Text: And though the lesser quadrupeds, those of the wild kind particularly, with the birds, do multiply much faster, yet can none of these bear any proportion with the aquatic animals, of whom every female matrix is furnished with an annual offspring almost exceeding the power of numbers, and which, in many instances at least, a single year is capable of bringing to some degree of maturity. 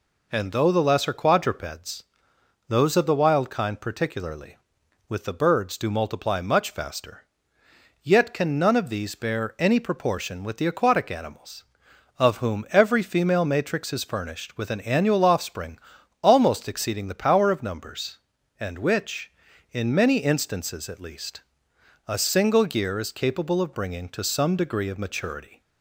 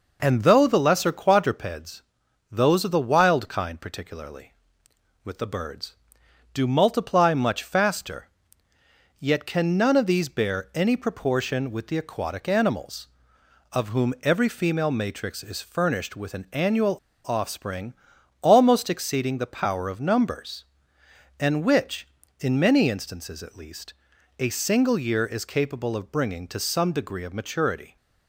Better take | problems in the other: first | pauses between "annual" and "offspring"; slight; at 16.9 s; 0.27 s long // pauses between "offspring" and "almost"; noticeable; at 17.9 s; 0.48 s long; noticeable in the first

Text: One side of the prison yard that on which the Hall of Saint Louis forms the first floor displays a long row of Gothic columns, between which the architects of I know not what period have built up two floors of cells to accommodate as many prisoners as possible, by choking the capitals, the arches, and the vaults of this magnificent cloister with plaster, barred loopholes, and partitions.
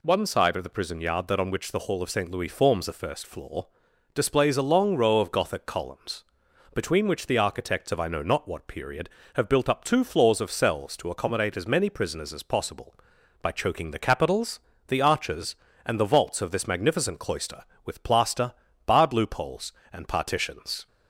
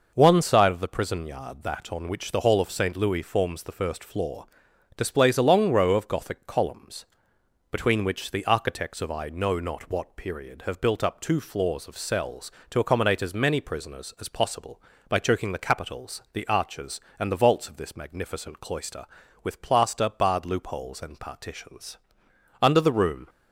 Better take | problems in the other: first | pauses between "floor" and "displays"; noticeable; at 4.4 s; 0.50 s long; noticeable in the first // goes on to say "Under the room"; noticeable; from 22.6 s on; 0.68 s long

